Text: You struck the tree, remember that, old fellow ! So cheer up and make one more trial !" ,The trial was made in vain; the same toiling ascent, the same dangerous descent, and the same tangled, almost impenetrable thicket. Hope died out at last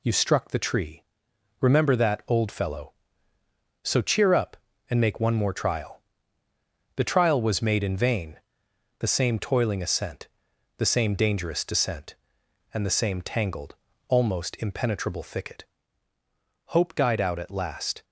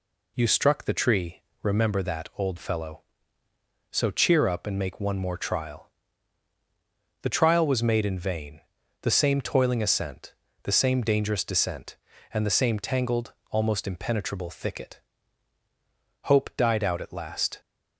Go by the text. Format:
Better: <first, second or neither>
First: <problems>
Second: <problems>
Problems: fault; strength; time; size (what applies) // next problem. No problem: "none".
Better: neither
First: none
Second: none